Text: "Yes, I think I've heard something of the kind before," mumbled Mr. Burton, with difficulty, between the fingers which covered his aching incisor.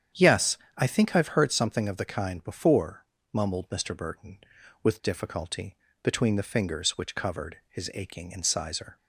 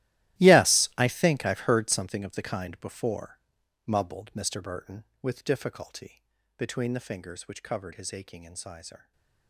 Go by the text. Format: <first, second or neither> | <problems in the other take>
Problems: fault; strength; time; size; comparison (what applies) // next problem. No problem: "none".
first | gets quieter; strong; throughout; 17.5 dB // starts louder than the rest; strong; until 1.4 s; 15 dB; strong in the first // stays silent after the last word; slight; from 8.9 s on; 0.5 s long